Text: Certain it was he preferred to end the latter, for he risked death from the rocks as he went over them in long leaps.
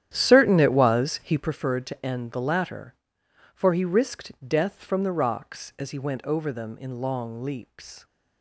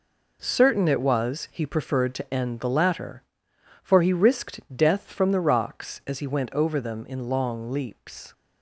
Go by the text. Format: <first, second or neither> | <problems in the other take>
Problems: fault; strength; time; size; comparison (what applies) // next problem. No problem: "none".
second | starts louder than the rest; strong; until 1.5 s; 10.5 dB // pauses between "risked" and "death"; slight; at 4.3 s; 0.16 s long; slight in the second